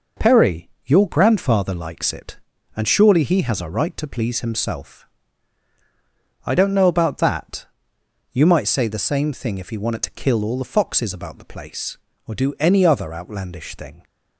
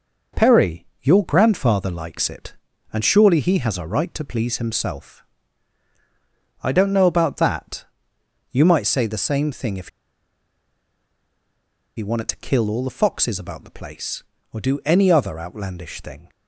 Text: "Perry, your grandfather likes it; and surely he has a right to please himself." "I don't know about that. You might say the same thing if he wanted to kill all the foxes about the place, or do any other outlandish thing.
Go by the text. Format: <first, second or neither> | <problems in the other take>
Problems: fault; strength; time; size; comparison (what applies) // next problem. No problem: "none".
first | pauses between "if" and "he"; strong; at 9.8 s; 2.0 s long